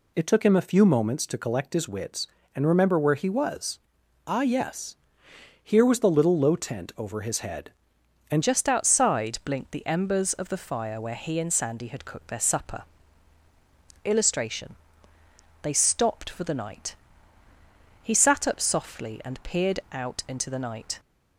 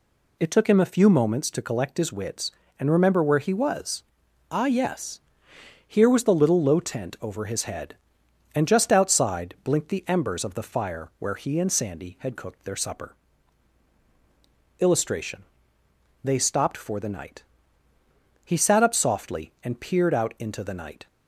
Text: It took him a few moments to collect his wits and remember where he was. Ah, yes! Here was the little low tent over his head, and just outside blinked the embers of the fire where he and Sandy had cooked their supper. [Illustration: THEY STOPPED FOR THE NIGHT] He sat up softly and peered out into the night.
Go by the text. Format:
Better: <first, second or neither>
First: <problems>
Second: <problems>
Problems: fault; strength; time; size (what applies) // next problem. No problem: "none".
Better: second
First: changes voice at "just"; from 8.4 s on; 12.5 s long // pauses between "NIGHT" and "He"; at 16.9 s; 1.0 s long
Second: pauses between "NIGHT" and "He"; at 17.4 s; 1.0 s long